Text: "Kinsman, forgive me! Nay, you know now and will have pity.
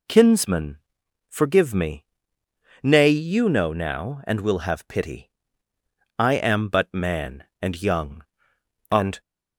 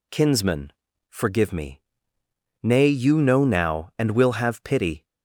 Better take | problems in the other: second | goes on to say "I am but man and young and"; strong; from 6.1 s on; 3.0 s long

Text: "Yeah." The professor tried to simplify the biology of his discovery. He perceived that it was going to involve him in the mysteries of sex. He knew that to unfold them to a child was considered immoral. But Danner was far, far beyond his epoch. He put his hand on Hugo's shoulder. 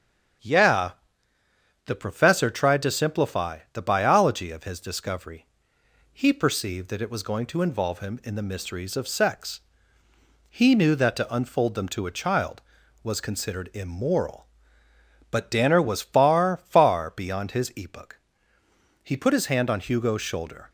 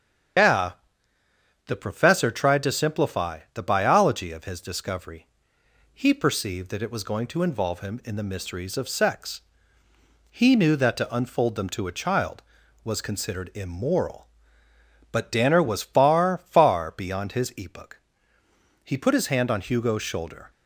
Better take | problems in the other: first | loses the start of "Yeah"; at 0.3 s; 145 ms // starts louder than the rest; strong; until 2.3 s; 8 dB; strong in the first

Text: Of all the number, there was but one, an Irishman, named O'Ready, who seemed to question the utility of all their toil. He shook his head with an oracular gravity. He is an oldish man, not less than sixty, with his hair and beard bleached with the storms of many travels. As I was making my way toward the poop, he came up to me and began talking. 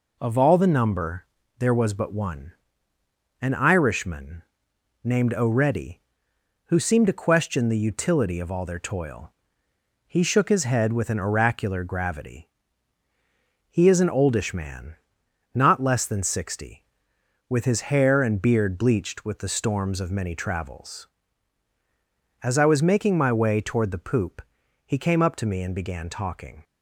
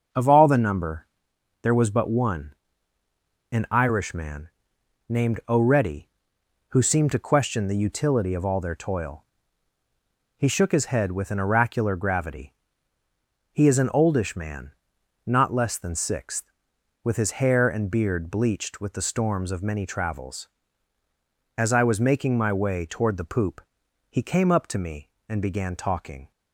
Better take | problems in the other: first | starts louder than the rest; until 1.6 s; 6.5 dB // says "sixth" for "sixty"; at 15.9 s

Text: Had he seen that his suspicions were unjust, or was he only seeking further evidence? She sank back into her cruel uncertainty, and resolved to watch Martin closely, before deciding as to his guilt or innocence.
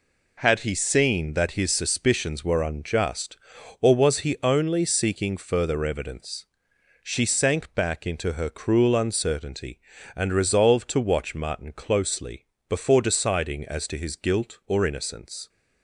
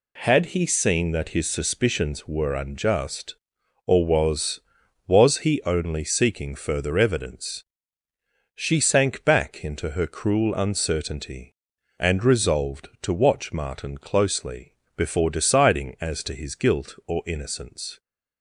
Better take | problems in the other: first | says "was" twice; at 5.0 s

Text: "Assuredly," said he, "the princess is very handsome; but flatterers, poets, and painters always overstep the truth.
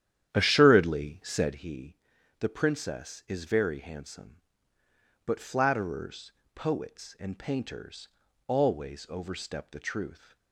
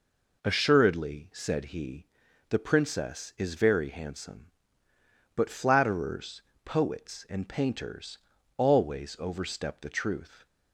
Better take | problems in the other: second | starts louder than the rest; strong; until 1.6 s; 10.5 dB // pauses between "painters" and "always"; at 8.0 s; 0.40 s long; also in the second

